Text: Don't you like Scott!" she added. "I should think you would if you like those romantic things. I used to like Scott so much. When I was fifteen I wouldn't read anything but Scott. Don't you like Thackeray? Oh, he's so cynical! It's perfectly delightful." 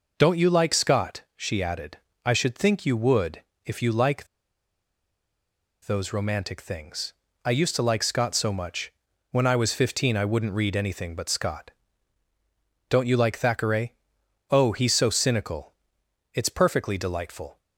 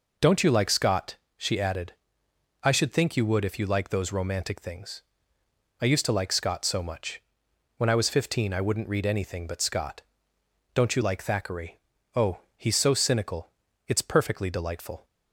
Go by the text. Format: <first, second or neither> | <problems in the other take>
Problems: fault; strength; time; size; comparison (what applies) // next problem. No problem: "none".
second | pauses between "would" and "if"; slight; at 3.4 s; 0.24 s long // pauses between "like" and "those"; strong; at 4.2 s; 1.5 s long